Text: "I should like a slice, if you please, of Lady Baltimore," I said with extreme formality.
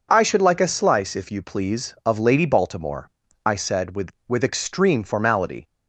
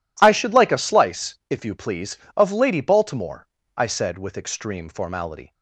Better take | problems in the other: second | says "with" twice; at 4.2 s

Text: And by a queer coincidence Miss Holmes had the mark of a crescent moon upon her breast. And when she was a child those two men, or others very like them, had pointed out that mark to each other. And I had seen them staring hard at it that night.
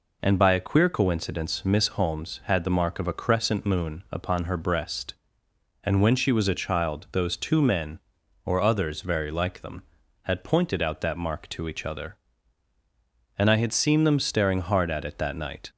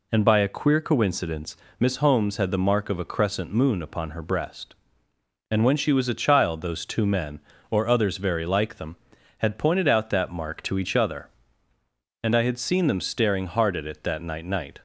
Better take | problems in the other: first | pauses between "coincidence" and "Miss"; slight; at 1.5 s; 0.24 s long // says "night" twice; at 14.4 s

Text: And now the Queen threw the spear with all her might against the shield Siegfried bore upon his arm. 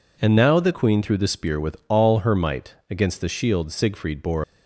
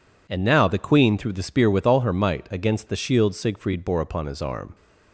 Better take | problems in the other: second | pauses between "might" and "against"; slight; at 2.7 s; 0.16 s long // stops before "upon his arm"; at 4.4 s

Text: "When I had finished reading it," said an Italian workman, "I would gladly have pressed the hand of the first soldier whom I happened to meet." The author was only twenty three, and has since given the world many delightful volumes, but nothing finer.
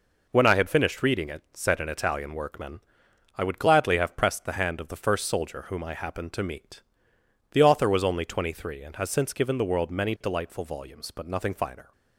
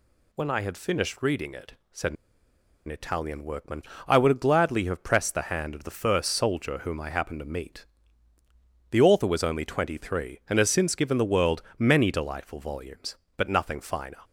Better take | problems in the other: first | pauses between "said" and "an"; noticeable; at 2.1 s; 0.72 s long // pauses between "world" and "many"; slight; at 11.5 s; 0.16 s long

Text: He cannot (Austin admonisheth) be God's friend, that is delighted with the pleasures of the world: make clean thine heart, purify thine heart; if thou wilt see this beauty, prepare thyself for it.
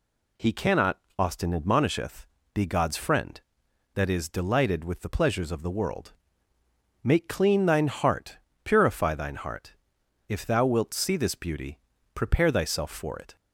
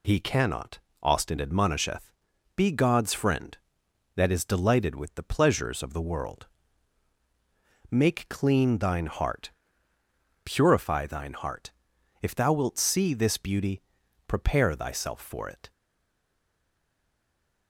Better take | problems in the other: first | stays silent after the last word; noticeable; from 15.7 s on; 1.9 s long

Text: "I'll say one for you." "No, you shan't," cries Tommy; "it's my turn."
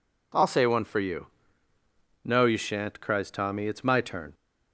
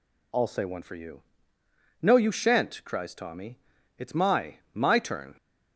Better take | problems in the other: first | says "my" twice; at 4.7 s

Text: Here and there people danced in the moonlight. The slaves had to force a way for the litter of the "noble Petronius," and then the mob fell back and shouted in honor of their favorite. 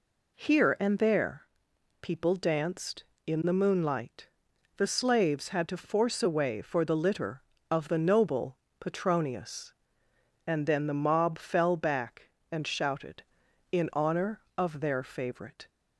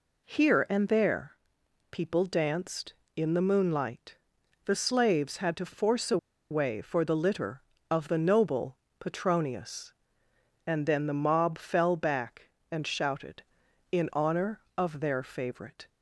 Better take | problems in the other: first | pauses between "there" and "people"; noticeable; at 1.3 s; 0.54 s long; noticeable in the first // pauses between "a" and "way"; slight; at 6.1 s; 0.34 s long // pauses between "noble" and "Petronius"; slight; at 8.7 s; 0.20 s long; slight in the first

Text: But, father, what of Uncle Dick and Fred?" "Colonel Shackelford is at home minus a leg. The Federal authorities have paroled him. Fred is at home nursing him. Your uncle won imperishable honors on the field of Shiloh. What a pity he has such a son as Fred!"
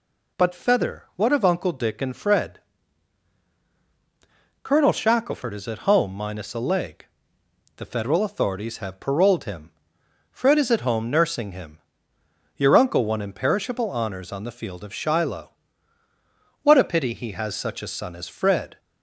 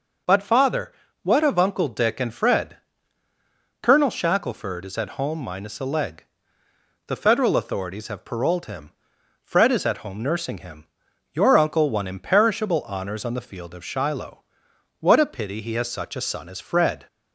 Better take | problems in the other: second | says "feather" for "father"; at 0.5 s

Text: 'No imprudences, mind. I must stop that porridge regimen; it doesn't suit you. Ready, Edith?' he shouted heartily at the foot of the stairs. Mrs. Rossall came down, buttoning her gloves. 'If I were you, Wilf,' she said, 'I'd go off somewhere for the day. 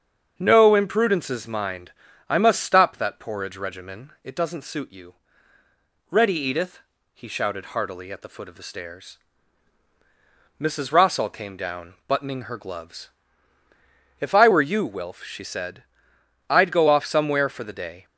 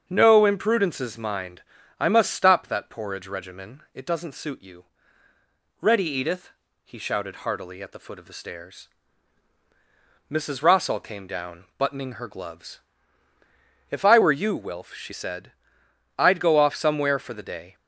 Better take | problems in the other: neither | starts louder than the rest; the same in both

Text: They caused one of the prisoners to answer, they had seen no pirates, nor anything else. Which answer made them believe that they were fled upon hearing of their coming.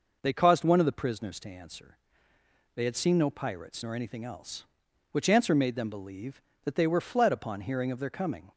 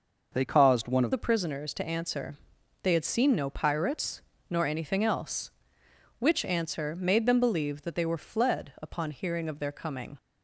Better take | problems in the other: first | changes voice at "the"; from 1.1 s on; 9.0 s long

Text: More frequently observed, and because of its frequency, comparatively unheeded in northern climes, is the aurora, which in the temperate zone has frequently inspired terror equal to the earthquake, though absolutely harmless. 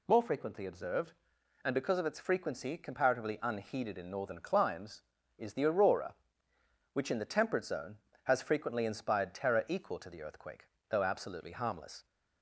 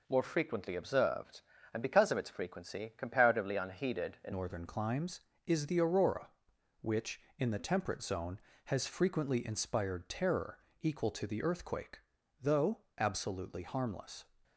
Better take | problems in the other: first | changes voice at "northern"; from 4.3 s on; 9.9 s long // pauses between "terror" and "equal"; slight; at 10.5 s; 0.20 s long // pauses between "though" and "absolutely"; slight; at 12.8 s; 0.16 s long

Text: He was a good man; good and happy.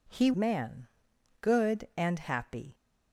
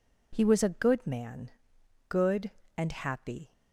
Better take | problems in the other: second | skips "was a good"; at 0.3 s

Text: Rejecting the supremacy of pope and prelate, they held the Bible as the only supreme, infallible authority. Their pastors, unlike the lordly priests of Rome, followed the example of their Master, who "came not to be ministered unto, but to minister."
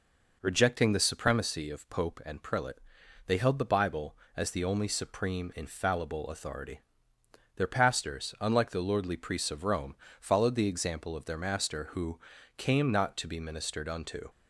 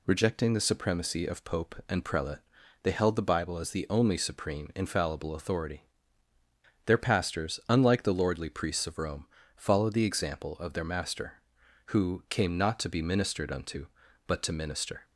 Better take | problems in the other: second | pauses between "who" and "came"; slight; at 12.2 s; 0.36 s long // stops before "but to minister"; at 14.2 s

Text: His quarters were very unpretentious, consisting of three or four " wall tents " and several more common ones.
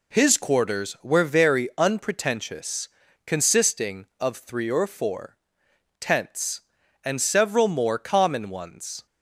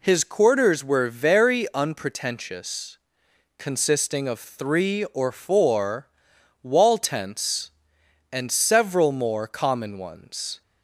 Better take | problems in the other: second | skips "wall"; at 6.0 s

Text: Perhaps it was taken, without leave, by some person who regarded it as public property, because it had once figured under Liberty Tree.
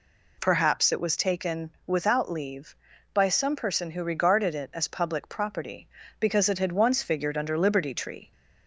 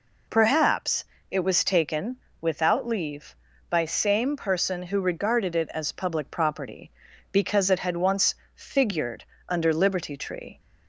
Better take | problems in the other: first | pauses between "Perhaps" and "it"; slight; at 1.0 s; 0.24 s long // says "same" for "some"; at 3.8 s // pauses between "once" and "figured"; slight; at 8.3 s; 0.18 s long // pauses between "figured" and "under"; slight; at 9.2 s; 0.24 s long

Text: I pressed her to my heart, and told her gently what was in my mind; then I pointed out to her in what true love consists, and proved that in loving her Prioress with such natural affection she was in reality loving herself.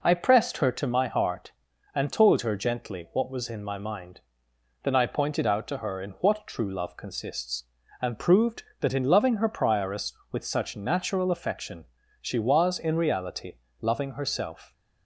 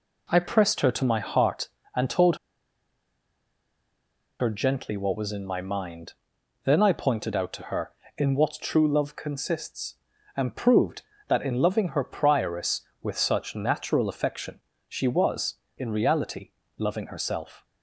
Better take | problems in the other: first | pauses between "told" and "her"; strong; at 2.3 s; 2.0 s long // pauses between "affection" and "she"; slight; at 14.6 s; 0.26 s long; slight in the first // pauses between "reality" and "loving"; slight; at 16.5 s; 0.28 s long; slight in the first

